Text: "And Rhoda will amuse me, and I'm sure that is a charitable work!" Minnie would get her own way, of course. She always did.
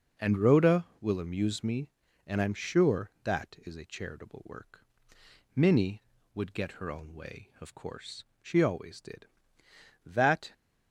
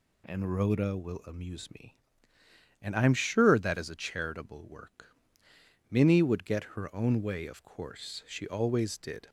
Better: second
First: goes on to say "That"; slight; from 10.0 s on; 0.46 s long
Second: none

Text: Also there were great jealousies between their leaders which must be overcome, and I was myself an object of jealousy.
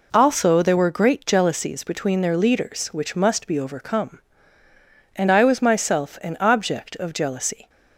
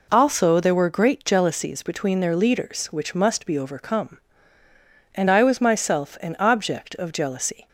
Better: neither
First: none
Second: none

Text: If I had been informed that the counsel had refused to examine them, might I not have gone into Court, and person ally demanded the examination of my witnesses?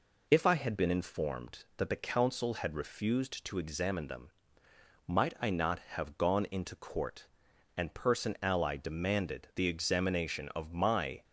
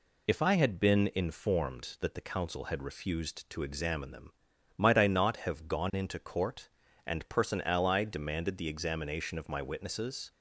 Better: second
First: stops before "witnesses"; at 11.2 s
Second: none

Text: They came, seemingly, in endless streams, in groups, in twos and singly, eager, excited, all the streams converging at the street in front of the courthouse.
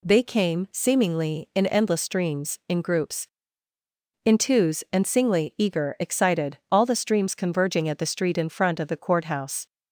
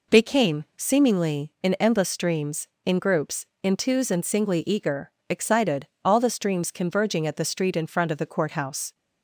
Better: neither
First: none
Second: none

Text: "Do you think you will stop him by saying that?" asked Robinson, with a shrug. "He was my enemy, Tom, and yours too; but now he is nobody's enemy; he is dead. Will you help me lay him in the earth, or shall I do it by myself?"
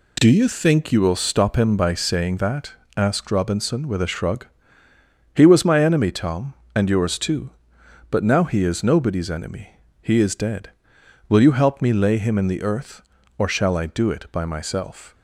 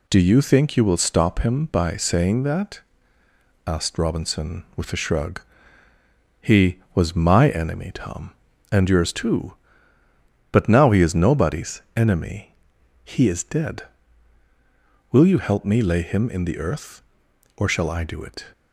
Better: first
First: none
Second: pauses between "nobody's" and "enemy"; slight; at 11.8 s; 0.16 s long // stops before "by myself"; at 18.5 s

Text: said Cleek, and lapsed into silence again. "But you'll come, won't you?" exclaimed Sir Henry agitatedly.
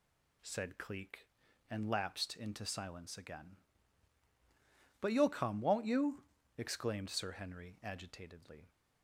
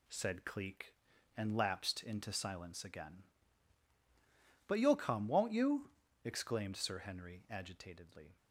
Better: first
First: none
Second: gets quieter; noticeable; throughout; 5.5 dB

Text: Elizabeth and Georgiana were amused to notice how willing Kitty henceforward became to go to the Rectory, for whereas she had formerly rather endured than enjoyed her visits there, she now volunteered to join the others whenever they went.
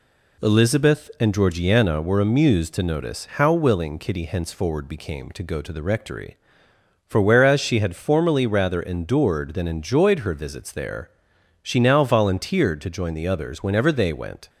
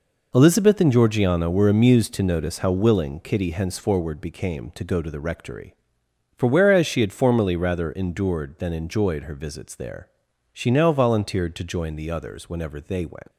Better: first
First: none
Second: leaves "went" unfinished; at 13.3 s; 155 ms

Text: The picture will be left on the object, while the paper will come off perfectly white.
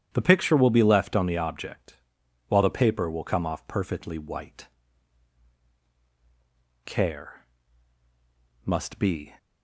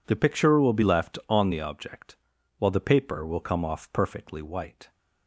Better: second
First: starts louder than the rest; strong; until 1.1 s; 10 dB // goes on to say "Care must be"; strong; from 6.8 s on; 2.5 s long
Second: none

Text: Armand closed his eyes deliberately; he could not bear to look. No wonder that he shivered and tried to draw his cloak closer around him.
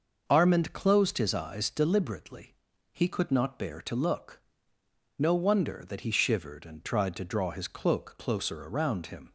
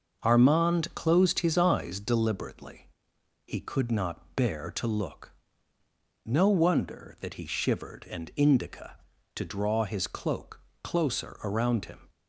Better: first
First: starts louder than the rest; noticeable; until 1.2 s; 6 dB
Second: starts louder than the rest; noticeable; until 1.2 s; 6 dB // says "indica" for "tried"; at 8.3 s // pauses between "cloak" and "closer"; slight; at 10.5 s; 0.24 s long

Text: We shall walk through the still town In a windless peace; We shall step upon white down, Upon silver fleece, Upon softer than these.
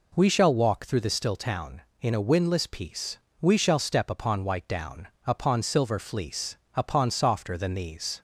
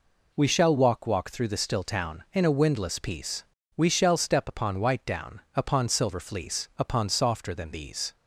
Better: first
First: none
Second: says "walk" twice; at 1.0 s

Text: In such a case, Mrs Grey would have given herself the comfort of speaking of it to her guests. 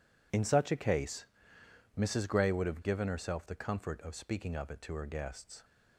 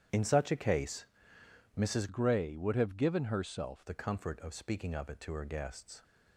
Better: first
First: none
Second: starts louder than the rest; strong; until 1.8 s; 9.5 dB // changes voice from "Grey" to "herself"; from 2.0 to 3.8 s; 1.8 s long

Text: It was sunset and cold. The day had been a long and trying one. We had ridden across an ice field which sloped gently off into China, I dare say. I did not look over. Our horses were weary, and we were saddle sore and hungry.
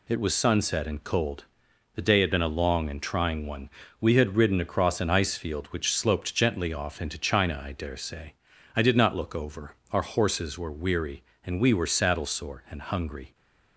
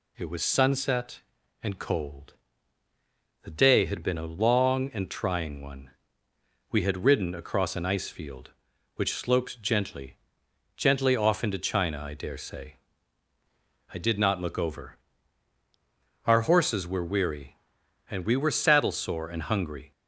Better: first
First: none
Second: says "gently" twice; at 10.7 s

